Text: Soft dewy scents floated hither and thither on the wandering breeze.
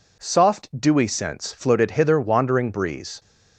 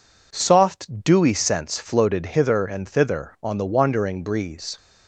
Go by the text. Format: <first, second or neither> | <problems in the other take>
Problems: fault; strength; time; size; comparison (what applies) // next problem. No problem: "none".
second | skips "and thither on the"; at 2.1 s